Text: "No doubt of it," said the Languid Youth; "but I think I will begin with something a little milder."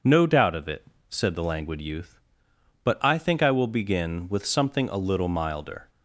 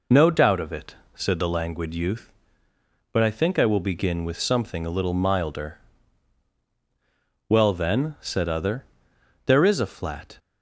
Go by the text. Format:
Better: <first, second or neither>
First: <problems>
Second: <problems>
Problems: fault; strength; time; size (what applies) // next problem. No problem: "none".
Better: first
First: none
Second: goes on to say "Well then said other there is a flat"; strong; from 7.4 s on; 2.9 s long